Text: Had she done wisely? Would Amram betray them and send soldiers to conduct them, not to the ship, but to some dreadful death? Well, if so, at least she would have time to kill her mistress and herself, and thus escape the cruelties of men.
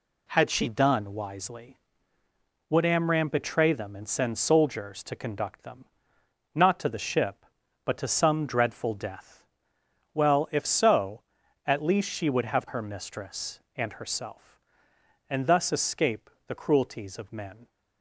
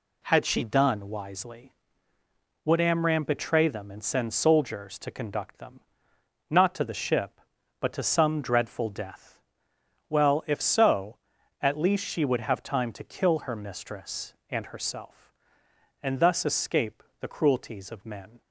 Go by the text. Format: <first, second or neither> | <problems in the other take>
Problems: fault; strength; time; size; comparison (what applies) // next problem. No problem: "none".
second | skips "time to kill"; at 12.6 s // pauses between "escape" and "the"; slight; at 16.2 s; 0.16 s long; slight in the second